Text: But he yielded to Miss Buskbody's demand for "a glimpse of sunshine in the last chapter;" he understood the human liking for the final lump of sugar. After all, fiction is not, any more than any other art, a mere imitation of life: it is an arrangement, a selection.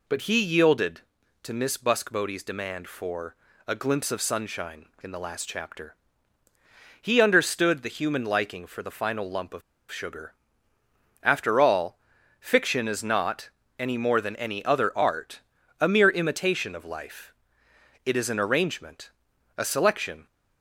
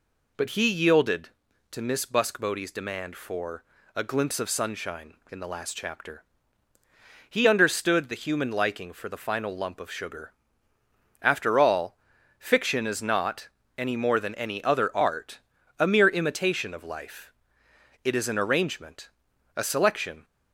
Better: second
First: pauses between "for" and "a"; slight; at 3.3 s; 0.32 s long // pauses between "of" and "sugar"; slight; at 9.6 s; 0.30 s long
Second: pauses between "for" and "a"; slight; at 3.6 s; 0.32 s long

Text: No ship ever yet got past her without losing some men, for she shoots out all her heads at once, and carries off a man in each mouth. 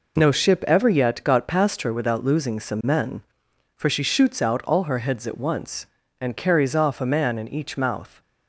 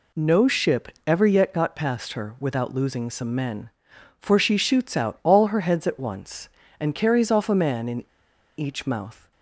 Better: first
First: none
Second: pauses between "ship" and "ever"; slight; at 0.8 s; 0.18 s long // pauses between "in" and "each"; noticeable; at 8.0 s; 0.53 s long

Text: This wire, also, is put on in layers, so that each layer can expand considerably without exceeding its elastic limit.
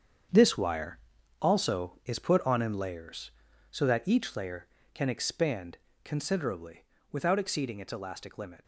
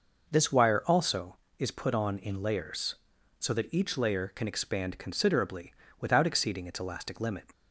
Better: second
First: gets quieter; strong; throughout; 10.5 dB // pauses between "expand" and "considerably"; slight; at 5.7 s; 0.24 s long // pauses between "considerably" and "without"; slight; at 6.8 s; 0.26 s long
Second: pauses between "considerably" and "without"; slight; at 5.7 s; 0.28 s long

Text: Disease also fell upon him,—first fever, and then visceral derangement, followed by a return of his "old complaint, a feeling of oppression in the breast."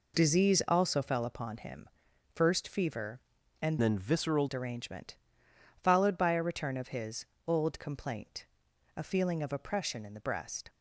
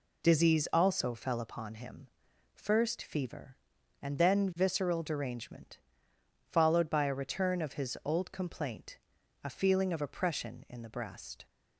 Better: second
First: changes voice from "then" to "visceral"; from 3.8 to 4.4 s; 0.6 s long // pauses between "his" and "old"; slight; at 7.2 s; 0.22 s long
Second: none

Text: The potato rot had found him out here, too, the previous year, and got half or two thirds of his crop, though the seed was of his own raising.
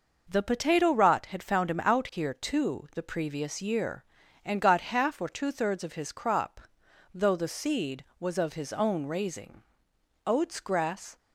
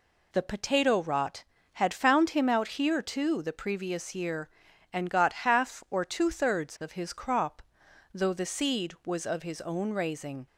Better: second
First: goes on to say "Oats grass"; noticeable; from 10.2 s on; 0.92 s long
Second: none

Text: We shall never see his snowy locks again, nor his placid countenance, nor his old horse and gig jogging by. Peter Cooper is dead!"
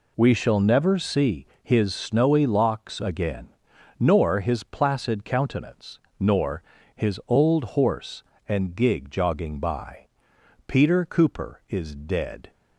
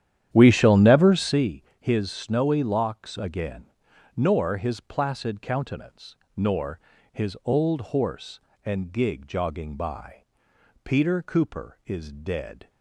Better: first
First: pauses between "see" and "his"; slight; at 1.4 s; 0.16 s long // pauses between "nor" and "his"; slight; at 6.6 s; 0.32 s long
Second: starts louder than the rest; strong; until 1.5 s; 10.5 dB // pauses between "see" and "his"; slight; at 1.6 s; 0.16 s long // pauses between "nor" and "his"; slight; at 6.7 s; 0.32 s long

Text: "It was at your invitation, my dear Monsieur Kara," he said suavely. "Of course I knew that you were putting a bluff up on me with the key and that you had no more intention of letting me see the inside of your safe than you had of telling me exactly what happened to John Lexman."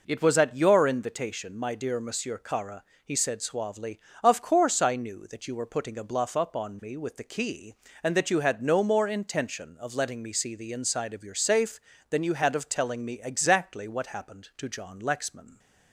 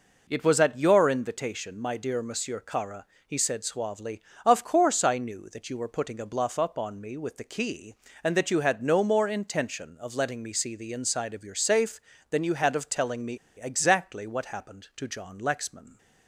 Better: first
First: none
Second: pauses between "me" and "exactly"; slight; at 13.3 s; 0.21 s long

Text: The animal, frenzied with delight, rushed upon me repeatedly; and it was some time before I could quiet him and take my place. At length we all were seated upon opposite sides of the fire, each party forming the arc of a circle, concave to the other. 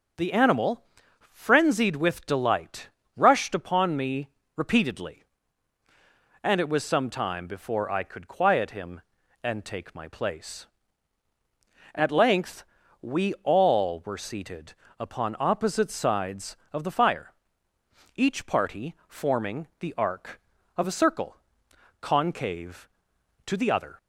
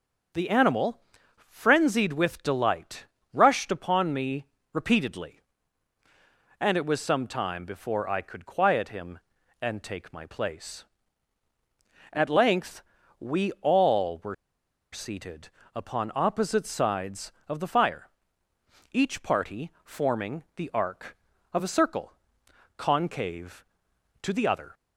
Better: first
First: starts louder than the rest; until 1.6 s; 6.5 dB // pauses between "me" and "repeatedly"; slight; at 4.2 s; 0.26 s long // pauses between "length" and "we"; at 12.6 s; 0.38 s long // pauses between "seated" and "upon"; slight; at 14.7 s; 0.26 s long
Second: starts louder than the rest; until 1.7 s; 7 dB // pauses between "me" and "repeatedly"; slight; at 4.4 s; 0.26 s long // pauses between "length" and "we"; at 12.8 s; 0.38 s long // pauses between "were" and "seated"; noticeable; at 14.3 s; 0.58 s long // pauses between "seated" and "upon"; slight; at 15.4 s; 0.26 s long

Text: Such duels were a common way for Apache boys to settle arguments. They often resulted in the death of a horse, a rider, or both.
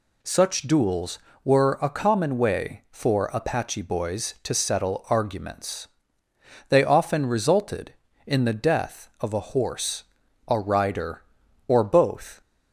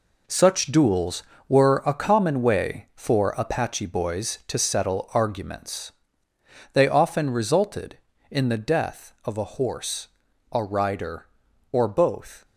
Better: first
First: none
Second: gets quieter; strong; throughout; 9.5 dB

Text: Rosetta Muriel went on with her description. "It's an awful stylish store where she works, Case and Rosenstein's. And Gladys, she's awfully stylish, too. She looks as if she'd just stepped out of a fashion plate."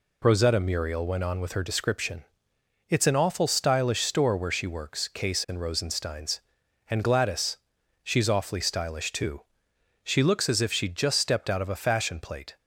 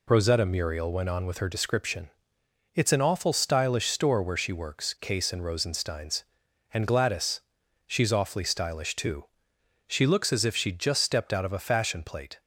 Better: neither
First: none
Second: none

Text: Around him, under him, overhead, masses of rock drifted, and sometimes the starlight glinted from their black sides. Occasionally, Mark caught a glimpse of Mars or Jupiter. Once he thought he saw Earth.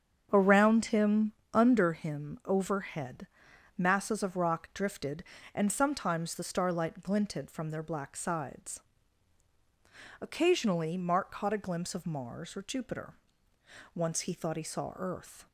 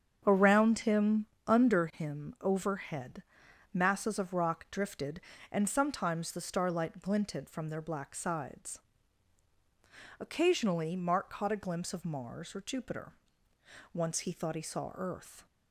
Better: neither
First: starts louder than the rest; strong; until 1.3 s; 7.5 dB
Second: starts louder than the rest; strong; until 1.2 s; 7.5 dB

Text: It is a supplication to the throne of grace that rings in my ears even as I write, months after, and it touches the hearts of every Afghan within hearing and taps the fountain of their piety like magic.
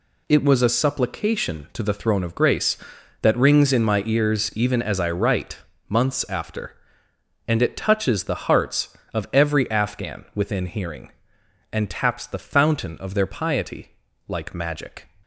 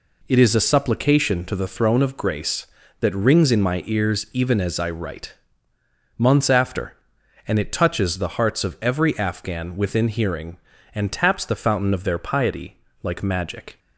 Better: second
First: says "was" for "is"; at 0.4 s // pauses between "piety" and "like"; slight; at 13.9 s; 0.36 s long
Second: pauses between "piety" and "like"; slight; at 12.7 s; 0.24 s long

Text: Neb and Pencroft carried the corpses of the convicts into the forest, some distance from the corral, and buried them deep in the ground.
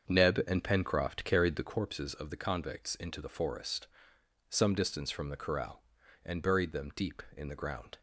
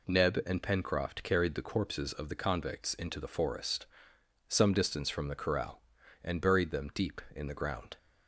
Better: second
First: starts louder than the rest; until 1.8 s; 7 dB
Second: none

